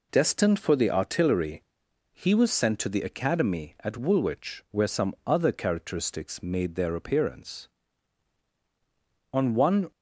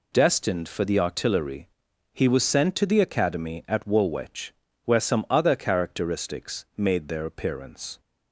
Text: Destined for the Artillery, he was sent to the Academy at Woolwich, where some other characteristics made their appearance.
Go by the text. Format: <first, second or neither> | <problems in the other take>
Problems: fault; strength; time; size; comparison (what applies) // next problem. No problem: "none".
second | goes on to say "On one"; from 9.3 s on; 0.58 s long